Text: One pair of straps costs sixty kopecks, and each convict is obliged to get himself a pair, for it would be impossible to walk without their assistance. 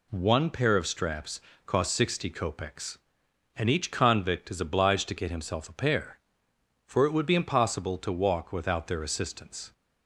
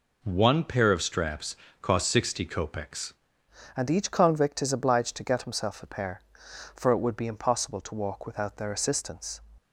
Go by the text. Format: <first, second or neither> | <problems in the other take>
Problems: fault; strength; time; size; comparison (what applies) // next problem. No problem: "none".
first | pauses between "straps" and "costs"; slight; at 1.5 s; 0.26 s long; slight in the first // changes voice at "and"; from 3.7 s on; 5.7 s long